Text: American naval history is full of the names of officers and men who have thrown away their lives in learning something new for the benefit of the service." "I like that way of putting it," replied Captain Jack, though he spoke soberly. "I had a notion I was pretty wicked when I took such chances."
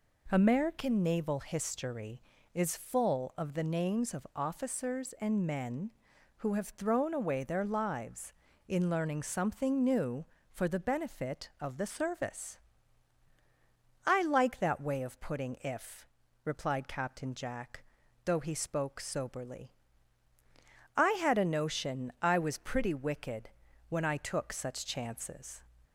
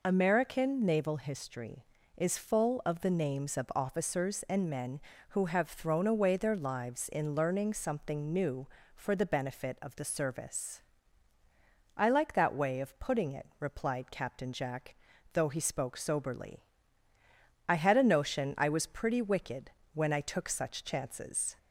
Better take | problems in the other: second | says "if" for "it"; at 15.6 s // pauses between "wicked" and "when"; at 23.5 s; 0.38 s long; slight in the second

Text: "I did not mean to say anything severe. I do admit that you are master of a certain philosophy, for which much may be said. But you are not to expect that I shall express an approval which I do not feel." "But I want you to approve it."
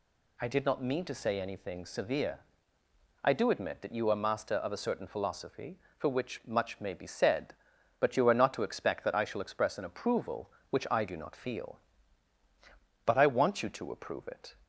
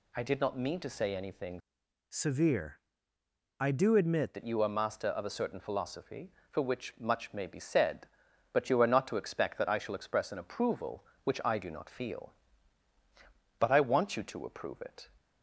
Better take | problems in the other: first | changes voice from "severe" to "admit"; from 2.0 to 4.3 s; 2.3 s long

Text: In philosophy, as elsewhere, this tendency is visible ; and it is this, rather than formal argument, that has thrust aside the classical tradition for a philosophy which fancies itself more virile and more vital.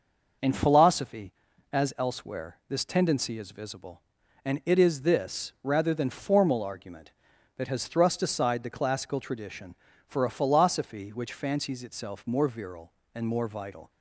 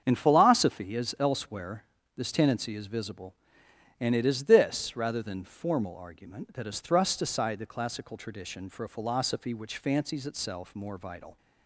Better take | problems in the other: first | starts louder than the rest; strong; until 1.0 s; 7.5 dB // skips "more virile and"; at 10.7 s

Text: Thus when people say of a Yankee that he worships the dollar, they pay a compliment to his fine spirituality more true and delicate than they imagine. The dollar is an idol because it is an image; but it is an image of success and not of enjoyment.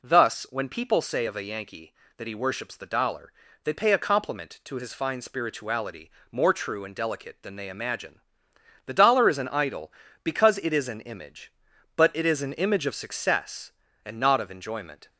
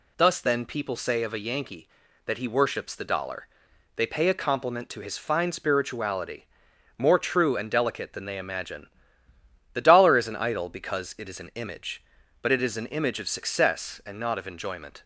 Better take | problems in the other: first | says "then" for "when"; at 0.4 s // pauses between "spirituality" and "more"; noticeable; at 6.4 s; 0.52 s long; slight in the first

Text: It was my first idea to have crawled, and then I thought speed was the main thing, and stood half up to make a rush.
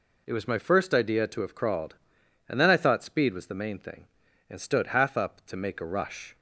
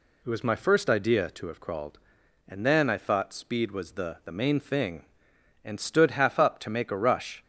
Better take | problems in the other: first | says "the" twice; at 4.2 s

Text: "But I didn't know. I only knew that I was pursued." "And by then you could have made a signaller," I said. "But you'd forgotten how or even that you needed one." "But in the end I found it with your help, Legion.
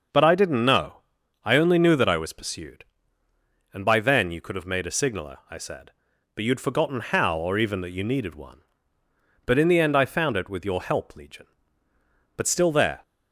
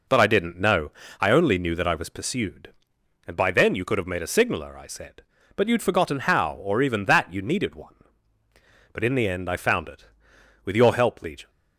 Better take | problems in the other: second | goes on to say "But still there"; noticeable; from 12.3 s on; 0.66 s long

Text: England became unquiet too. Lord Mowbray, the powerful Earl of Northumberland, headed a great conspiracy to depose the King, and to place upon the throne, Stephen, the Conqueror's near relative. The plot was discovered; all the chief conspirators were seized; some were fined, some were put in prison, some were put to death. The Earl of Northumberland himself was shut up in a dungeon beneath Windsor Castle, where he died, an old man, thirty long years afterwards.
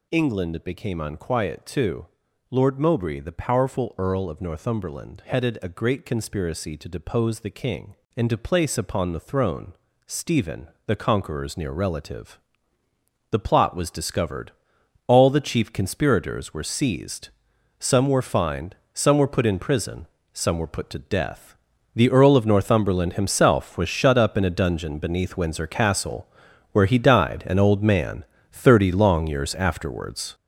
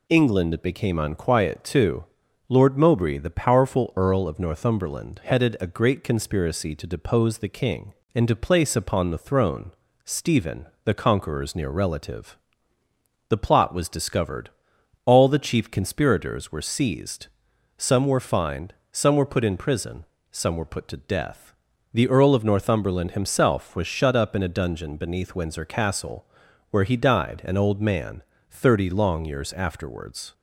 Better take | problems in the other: second | gets louder; strong; throughout; 8 dB

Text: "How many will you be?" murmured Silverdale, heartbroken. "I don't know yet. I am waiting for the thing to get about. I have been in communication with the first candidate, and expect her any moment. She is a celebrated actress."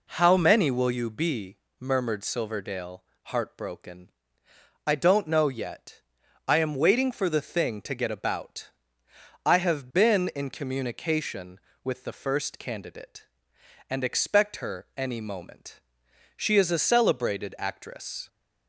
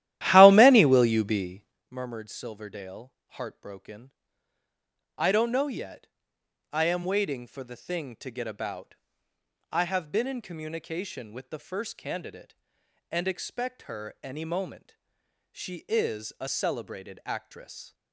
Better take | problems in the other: first | starts louder than the rest; strong; until 1.8 s; 13.5 dB

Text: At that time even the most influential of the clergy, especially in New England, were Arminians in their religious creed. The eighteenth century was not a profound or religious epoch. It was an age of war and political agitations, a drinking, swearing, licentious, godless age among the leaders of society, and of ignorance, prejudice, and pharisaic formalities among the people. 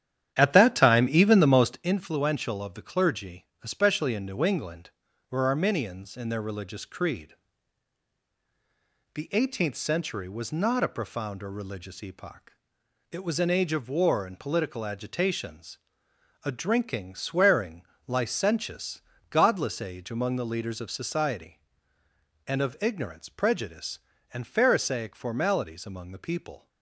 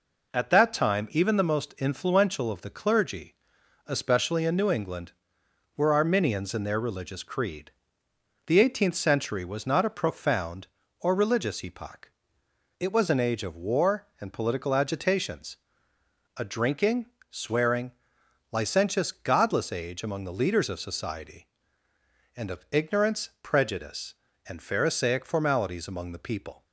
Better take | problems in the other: second | starts louder than the rest; strong; until 2.0 s; 10 dB

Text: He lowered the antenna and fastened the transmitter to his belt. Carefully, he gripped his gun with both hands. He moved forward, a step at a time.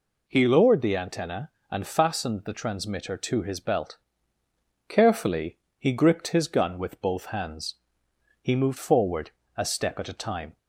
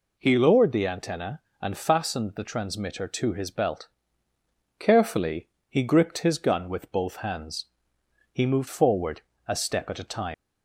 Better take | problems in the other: first | leaves "time" unfinished; at 10.3 s; 140 ms

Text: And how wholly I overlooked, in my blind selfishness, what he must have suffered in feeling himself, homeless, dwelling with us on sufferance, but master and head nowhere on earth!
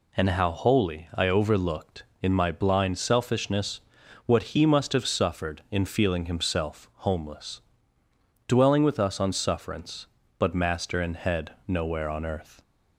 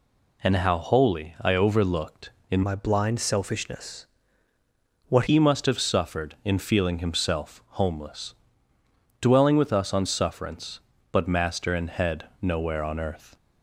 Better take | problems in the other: first | changes voice from "my" to "what"; from 2.6 to 5.2 s; 2.6 s long

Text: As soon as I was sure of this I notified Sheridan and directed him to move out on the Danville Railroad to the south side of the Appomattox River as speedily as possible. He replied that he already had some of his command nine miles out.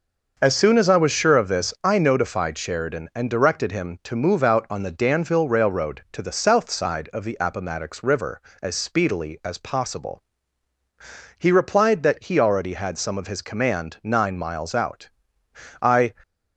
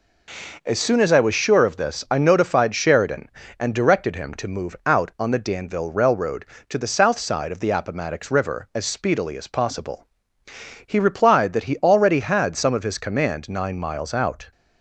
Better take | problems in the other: second | starts louder than the rest; until 1.3 s; 6 dB // goes on to say "I"; slight; from 15.8 s on; 0.32 s long

